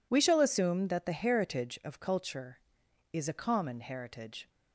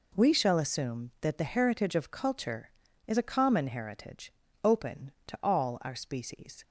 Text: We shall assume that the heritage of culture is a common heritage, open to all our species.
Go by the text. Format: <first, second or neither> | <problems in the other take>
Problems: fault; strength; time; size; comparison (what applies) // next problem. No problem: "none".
second | stops before "open to all our species"; at 4.4 s